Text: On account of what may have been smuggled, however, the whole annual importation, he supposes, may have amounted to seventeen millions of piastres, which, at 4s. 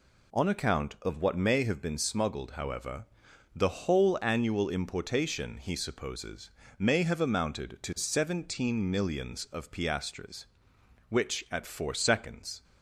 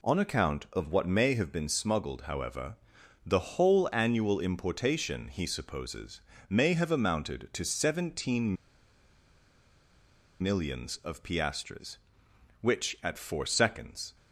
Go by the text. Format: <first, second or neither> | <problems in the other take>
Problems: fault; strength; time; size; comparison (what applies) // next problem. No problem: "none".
first | pauses between "seventeen" and "millions"; strong; at 8.5 s; 1.8 s long